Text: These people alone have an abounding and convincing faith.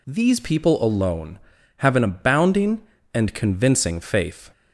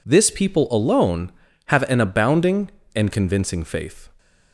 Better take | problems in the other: first | says "This" for "These"; at 0.0 s

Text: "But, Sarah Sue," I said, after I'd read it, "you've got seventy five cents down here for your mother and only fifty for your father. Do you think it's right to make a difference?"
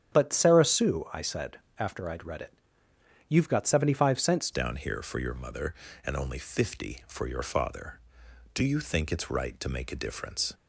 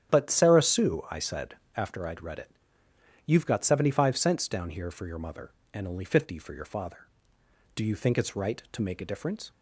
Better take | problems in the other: second | starts louder than the rest; strong; until 1.1 s; 9.5 dB; strong in the second // changes voice at "down"; from 4.5 s on; 6.0 s long

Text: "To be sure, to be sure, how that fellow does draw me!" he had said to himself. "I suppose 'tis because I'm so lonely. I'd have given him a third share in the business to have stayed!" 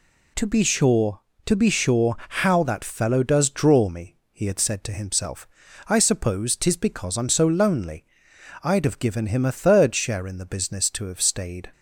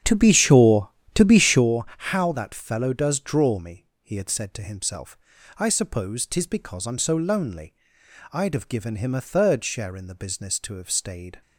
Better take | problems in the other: first | starts louder than the rest; strong; until 1.7 s; 9 dB

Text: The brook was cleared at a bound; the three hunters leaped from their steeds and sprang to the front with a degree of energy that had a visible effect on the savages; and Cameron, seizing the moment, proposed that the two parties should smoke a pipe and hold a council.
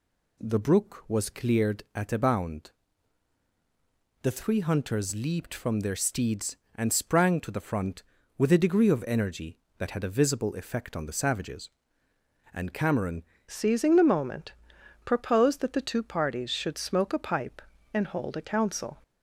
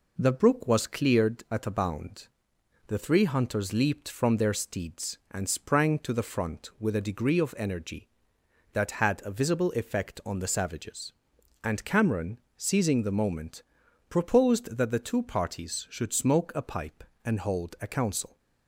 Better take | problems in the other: second | changes voice at "seizing"; from 13.4 s on; 5.6 s long

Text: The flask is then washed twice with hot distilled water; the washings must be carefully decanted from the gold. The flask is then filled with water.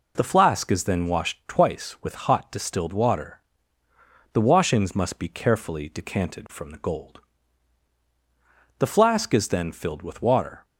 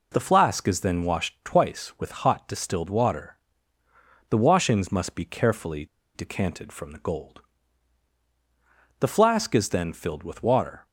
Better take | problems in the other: first | pauses between "carefully" and "decanted"; slight; at 5.8 s; 0.28 s long

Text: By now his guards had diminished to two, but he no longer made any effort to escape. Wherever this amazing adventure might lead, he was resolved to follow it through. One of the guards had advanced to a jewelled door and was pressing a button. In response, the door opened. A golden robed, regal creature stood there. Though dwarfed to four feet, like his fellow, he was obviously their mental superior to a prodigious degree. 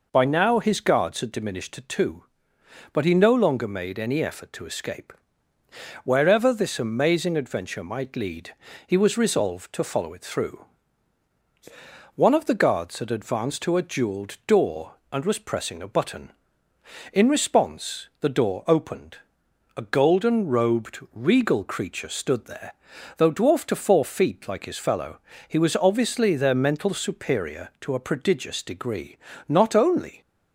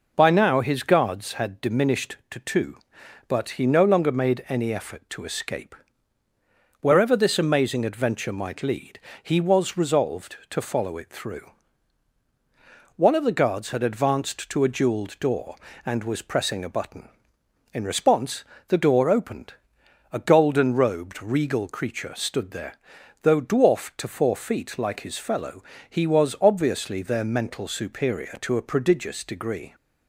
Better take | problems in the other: second | goes on to say "Not only"; noticeable; from 29.4 s on; 0.72 s long

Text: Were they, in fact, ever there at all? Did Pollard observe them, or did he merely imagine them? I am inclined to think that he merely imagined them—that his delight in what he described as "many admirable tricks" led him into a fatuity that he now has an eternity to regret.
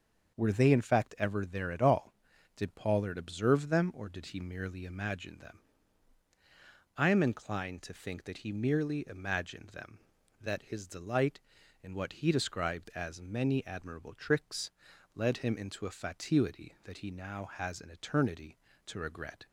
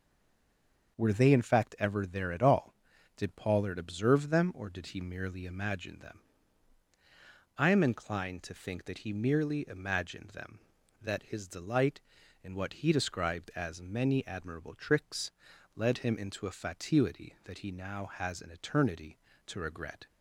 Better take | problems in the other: first | stays silent before the first word; slight; until 0.9 s; 0.9 s long // starts louder than the rest; until 2.0 s; 6.5 dB; also in the first // pauses between "tricks" and "led"; at 15.3 s; 0.42 s long; also in the first

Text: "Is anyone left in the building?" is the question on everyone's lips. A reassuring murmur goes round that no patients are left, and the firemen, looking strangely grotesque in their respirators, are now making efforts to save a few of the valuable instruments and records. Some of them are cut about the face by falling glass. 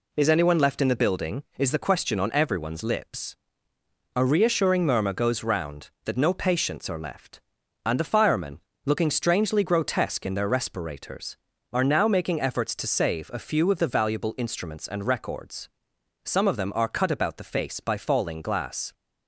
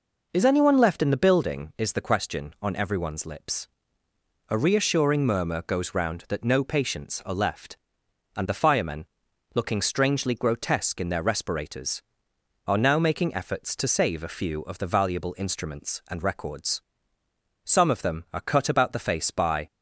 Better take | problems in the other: first | stops before "falling glass"; at 19.6 s

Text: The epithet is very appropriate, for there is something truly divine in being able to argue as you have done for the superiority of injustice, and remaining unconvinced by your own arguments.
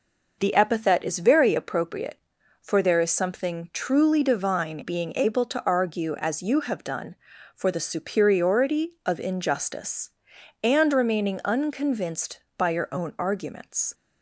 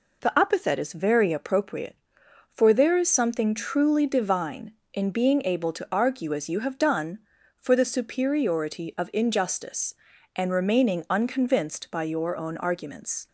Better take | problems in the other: second | skips "in"; at 4.8 s

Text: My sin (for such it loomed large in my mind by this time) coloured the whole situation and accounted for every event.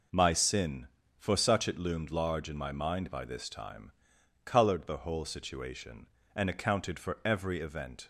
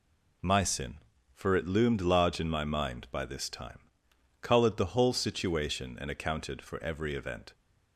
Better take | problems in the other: first | skips "such"; at 1.5 s

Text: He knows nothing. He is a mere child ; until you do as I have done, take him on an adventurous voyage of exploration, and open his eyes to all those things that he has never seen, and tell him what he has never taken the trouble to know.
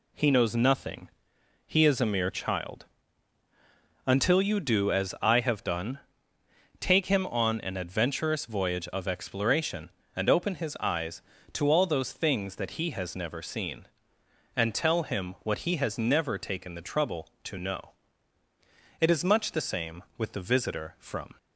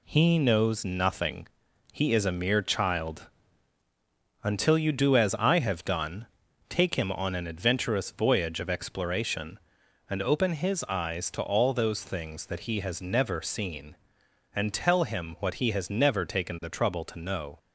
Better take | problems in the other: second | goes on to say "It is much the same with the visitor from"; strong; from 19.0 s on; 2.3 s long

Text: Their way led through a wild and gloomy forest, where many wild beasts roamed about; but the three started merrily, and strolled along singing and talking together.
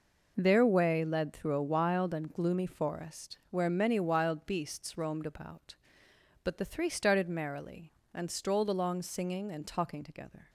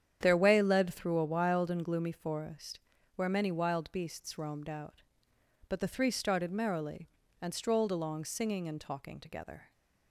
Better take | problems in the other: first | starts louder than the rest; strong; until 1.2 s; 9 dB // says "out" for "about"; at 4.6 s

